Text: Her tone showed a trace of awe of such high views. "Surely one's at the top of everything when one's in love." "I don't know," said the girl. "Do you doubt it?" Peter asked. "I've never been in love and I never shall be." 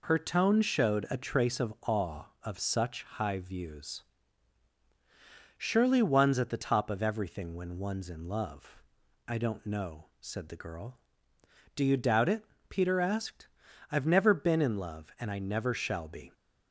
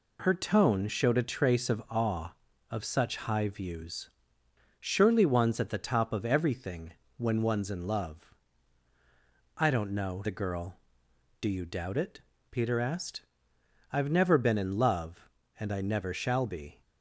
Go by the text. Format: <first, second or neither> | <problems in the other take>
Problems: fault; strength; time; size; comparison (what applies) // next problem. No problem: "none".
first | pauses between "everything" and "when"; slight; at 6.9 s; 0.24 s long // skips "said"; at 10.2 s